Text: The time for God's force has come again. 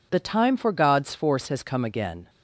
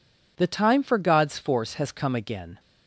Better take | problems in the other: neither | none

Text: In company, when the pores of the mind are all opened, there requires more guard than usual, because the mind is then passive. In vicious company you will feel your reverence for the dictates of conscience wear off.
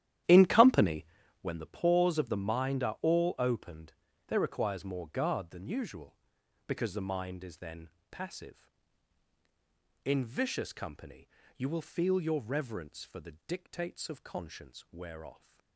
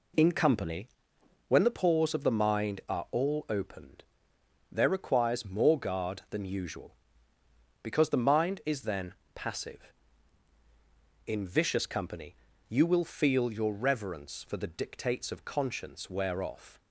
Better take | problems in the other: second | starts louder than the rest; strong; until 1.5 s; 12 dB // pauses between "then" and "passive"; slight; at 7.9 s; 0.20 s long; slight in the second // pauses between "company" and "you"; slight; at 11.2 s; 0.28 s long; slight in the second

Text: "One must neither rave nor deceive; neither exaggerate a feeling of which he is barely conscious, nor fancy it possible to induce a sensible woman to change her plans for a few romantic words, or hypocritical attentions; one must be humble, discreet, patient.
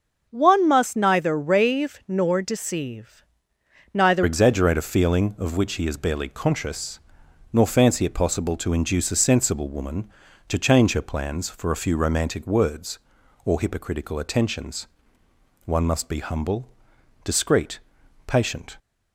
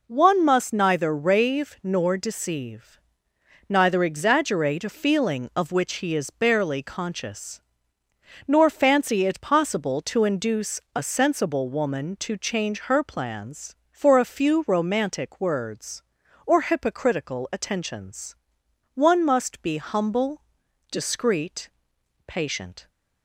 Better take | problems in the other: second | starts louder than the rest; until 1.3 s; 6 dB // changes voice at "exaggerate"; from 4.2 s on; 14.5 s long

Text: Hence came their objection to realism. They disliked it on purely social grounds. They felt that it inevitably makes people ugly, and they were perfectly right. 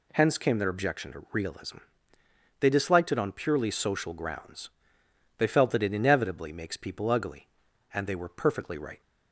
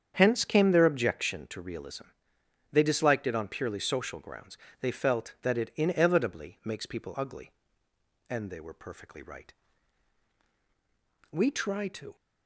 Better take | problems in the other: first | starts louder than the rest; strong; until 1.1 s; 8 dB // goes on to say "We try to"; noticeable; from 11.3 s on; 0.82 s long

